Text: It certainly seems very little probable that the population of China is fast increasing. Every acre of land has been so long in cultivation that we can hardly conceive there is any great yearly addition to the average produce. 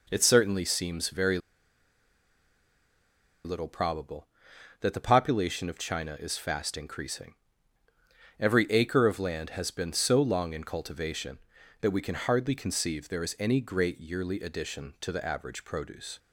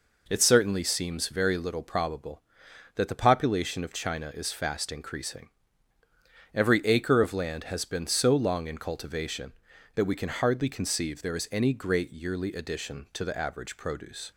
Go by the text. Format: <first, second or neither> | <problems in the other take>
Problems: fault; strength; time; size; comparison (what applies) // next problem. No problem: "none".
second | pauses between "very" and "little"; strong; at 1.3 s; 2.0 s long